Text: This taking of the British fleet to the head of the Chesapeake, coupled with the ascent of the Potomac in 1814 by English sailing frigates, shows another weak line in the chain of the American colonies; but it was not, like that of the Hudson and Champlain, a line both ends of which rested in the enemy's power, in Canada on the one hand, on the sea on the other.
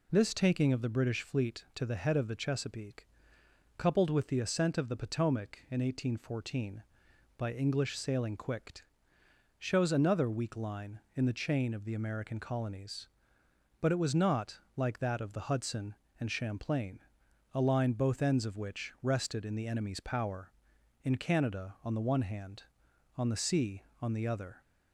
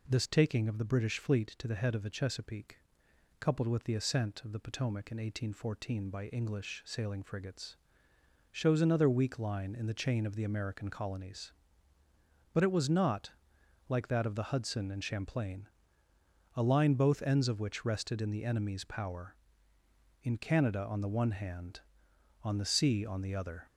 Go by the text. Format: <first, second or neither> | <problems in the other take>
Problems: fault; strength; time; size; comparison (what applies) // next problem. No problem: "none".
second | says "quicked" for "frigates"; at 8.3 s